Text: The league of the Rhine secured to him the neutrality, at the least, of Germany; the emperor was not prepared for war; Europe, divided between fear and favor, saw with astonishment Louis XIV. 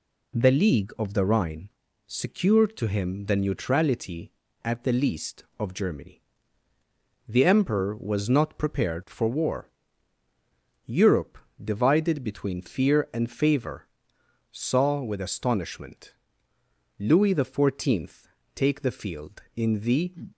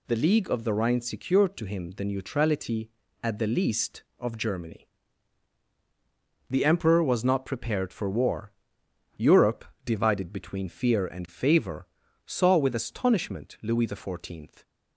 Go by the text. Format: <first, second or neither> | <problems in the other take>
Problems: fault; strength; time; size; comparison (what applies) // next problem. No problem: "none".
second | pauses between "Rhine" and "secured"; at 1.6 s; 0.40 s long // pauses between "astonishment" and "Louis"; noticeable; at 16.1 s; 0.86 s long // goes on to say "take the field in the"; from 18.5 s on; 1.6 s long